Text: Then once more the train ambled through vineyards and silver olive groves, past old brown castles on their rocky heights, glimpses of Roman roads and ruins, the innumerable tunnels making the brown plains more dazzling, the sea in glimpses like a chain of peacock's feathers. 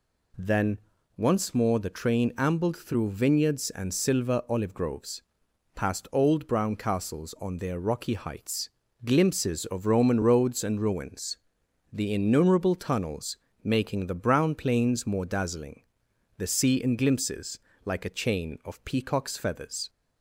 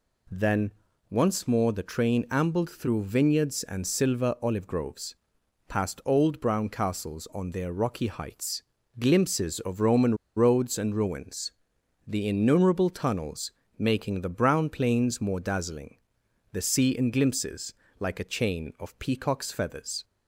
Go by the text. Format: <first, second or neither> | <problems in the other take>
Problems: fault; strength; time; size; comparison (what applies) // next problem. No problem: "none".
first | pauses between "Then" and "once"; at 0.7 s; 0.38 s long; also in the first // pauses between "Roman" and "roads"; slight; at 10.1 s; 0.22 s long // pauses between "tunnels" and "making"; slight; at 13.5 s; 0.26 s long; slight in the first // pauses between "glimpses" and "like"; slight; at 17.7 s; 0.26 s long; slight in the first